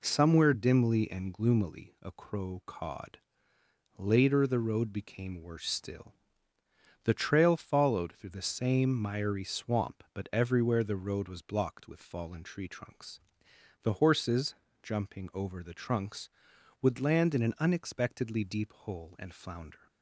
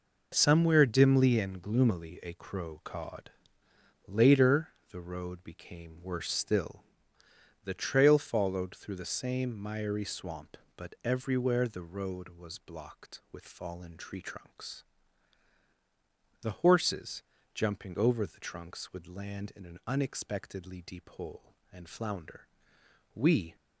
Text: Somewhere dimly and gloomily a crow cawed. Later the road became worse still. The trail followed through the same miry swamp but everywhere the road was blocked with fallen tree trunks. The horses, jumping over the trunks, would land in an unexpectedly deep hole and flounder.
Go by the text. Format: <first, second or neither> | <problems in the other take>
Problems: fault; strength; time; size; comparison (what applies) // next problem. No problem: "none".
first | pauses between "Later" and "the"; slight; at 4.6 s; 0.20 s long // goes on to say "We"; slight; from 23.1 s on; 0.42 s long